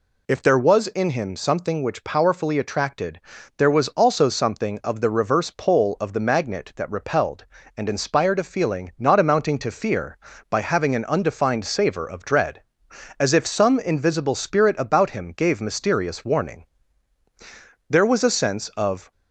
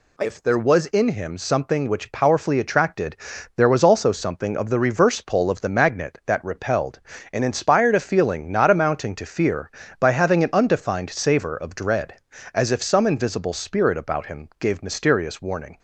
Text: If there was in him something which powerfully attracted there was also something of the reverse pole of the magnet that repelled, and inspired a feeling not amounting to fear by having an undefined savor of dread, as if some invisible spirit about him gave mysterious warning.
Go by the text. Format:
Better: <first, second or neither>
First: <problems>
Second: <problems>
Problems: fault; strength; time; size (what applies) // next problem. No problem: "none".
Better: second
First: pauses between "attracted" and "there"; at 3.2 s; 0.38 s long // goes on to say "There was a sense of"; noticeable; from 17.8 s on; 1.2 s long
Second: pauses between "attracted" and "there"; at 3.1 s; 0.40 s long